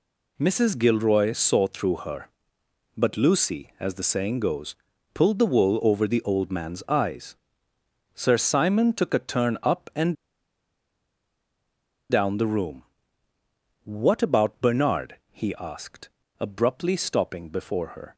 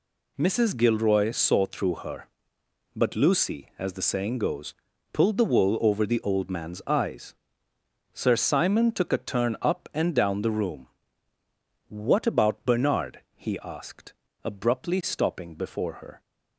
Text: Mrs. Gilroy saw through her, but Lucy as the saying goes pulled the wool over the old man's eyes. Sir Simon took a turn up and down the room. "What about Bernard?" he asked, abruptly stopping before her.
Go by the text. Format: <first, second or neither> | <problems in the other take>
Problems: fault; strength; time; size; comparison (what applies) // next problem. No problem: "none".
second | pauses between "goes" and "pulled"; at 4.7 s; 0.38 s long; also in the second // pauses between "and" and "down"; strong; at 10.1 s; 1.9 s long